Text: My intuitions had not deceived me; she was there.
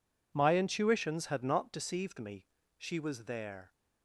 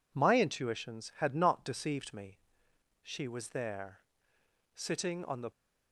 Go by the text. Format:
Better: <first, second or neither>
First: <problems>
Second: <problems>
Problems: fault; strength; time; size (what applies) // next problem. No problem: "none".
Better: first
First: none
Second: goes on to say "Sitting on the"; noticeable; from 4.7 s on; 0.76 s long